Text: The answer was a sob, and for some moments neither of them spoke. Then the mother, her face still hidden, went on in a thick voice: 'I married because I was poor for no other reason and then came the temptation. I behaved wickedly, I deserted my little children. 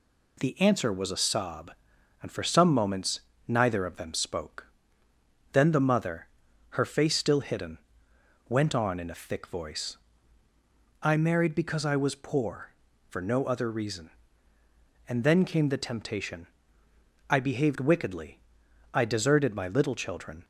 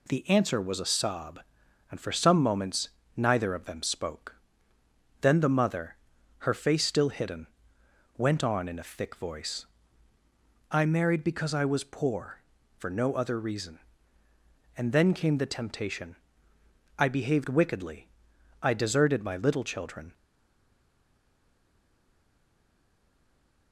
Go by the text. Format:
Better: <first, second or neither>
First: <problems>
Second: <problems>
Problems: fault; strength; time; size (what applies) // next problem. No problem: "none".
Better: first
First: pauses between "moments" and "neither"; slight; at 3.2 s; 0.28 s long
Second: pauses between "moments" and "neither"; slight; at 2.8 s; 0.28 s long // stays silent after the last word; strong; from 20.1 s on; 3.6 s long